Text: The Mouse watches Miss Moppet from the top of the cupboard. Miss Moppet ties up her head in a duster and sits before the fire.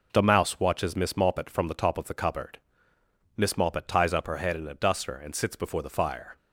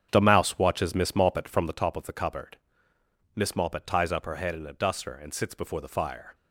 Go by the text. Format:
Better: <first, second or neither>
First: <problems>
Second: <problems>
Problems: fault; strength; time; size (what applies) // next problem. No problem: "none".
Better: first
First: none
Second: starts louder than the rest; strong; until 1.8 s; 8 dB